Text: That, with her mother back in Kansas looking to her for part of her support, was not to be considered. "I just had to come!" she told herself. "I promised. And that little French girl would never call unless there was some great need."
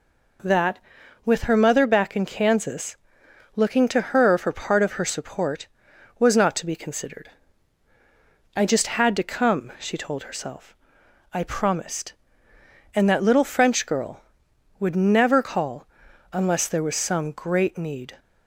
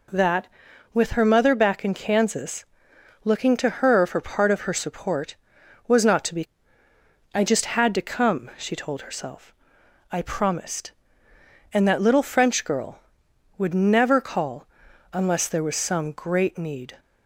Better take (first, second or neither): first